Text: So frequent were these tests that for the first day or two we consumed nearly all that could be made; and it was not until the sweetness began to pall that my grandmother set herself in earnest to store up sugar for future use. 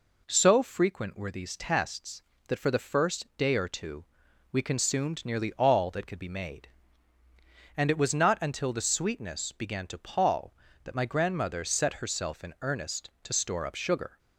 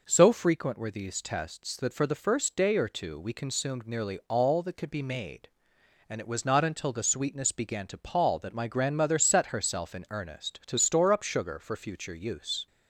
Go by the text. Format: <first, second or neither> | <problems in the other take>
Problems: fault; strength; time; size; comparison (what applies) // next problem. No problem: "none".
second | pauses between "two" and "we"; noticeable; at 4.0 s; 0.48 s long // stops before "for future use"; at 14.1 s